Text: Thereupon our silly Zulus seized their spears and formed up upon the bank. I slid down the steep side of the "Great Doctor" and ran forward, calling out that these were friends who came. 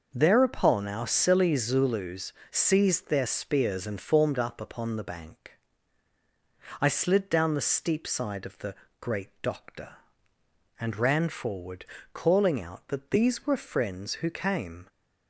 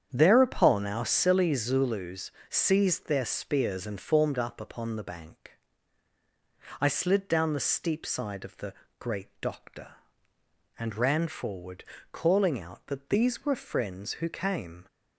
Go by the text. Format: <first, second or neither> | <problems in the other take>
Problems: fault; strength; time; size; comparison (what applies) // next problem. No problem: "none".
first | starts louder than the rest; strong; until 1.2 s; 8.5 dB // pauses between "Zulus" and "seized"; slight; at 2.3 s; 0.18 s long; slight in the first // pauses between "the" and "Great"; slight; at 8.7 s; 0.26 s long; slight in the first